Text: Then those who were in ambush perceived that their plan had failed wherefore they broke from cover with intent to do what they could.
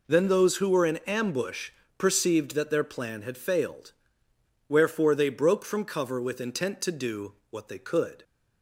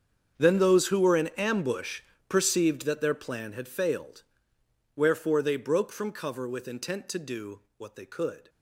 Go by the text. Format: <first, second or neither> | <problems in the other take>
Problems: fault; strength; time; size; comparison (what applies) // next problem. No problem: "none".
first | gets quieter; strong; throughout; 18 dB // pauses between "ambush" and "perceived"; slight; at 2.0 s; 0.26 s long; slight in the first // pauses between "failed" and "wherefore"; noticeable; at 4.2 s; 0.74 s long; noticeable in the first // pauses between "do" and "what"; slight; at 7.5 s; 0.16 s long; slight in the first